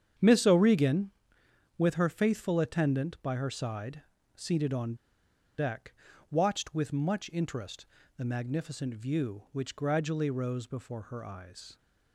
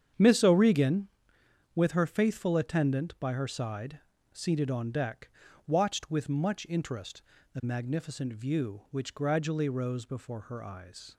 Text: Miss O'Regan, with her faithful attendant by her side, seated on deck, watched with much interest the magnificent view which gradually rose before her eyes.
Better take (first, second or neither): second